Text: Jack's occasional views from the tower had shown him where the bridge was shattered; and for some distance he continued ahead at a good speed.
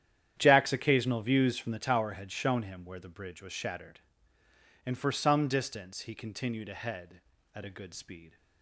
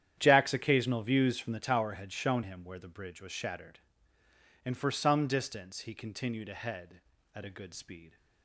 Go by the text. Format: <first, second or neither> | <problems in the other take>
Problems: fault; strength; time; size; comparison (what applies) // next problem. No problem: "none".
neither | starts louder than the rest; strong; the same in both